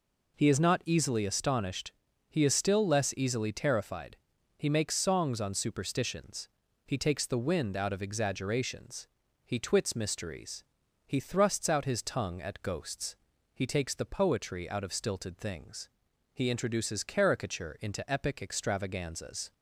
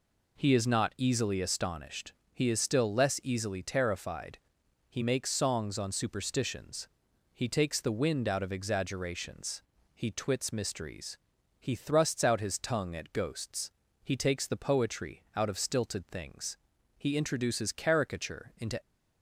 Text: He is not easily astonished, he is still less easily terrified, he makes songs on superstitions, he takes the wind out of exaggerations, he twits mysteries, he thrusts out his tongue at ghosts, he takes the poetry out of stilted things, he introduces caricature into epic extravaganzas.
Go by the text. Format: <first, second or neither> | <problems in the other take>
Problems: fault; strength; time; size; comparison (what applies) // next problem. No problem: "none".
first | stops before "epic extravaganzas"; at 18.8 s